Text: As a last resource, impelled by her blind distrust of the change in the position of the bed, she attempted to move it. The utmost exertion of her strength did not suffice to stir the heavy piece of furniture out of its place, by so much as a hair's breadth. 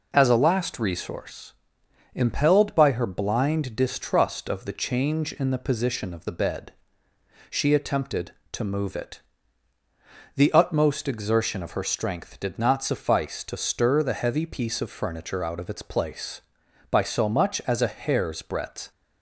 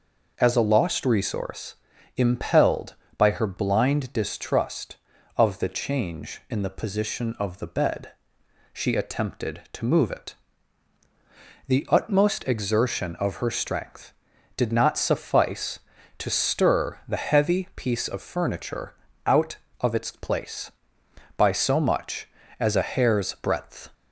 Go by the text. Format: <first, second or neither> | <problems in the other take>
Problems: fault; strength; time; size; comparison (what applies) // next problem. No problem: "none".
first | says "lost" for "last"; at 0.6 s // pauses between "furniture" and "out"; slight; at 18.9 s; 0.32 s long